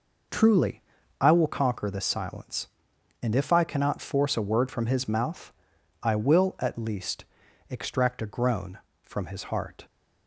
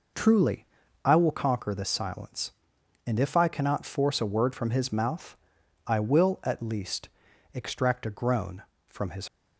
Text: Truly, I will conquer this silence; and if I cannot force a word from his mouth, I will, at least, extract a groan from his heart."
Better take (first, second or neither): first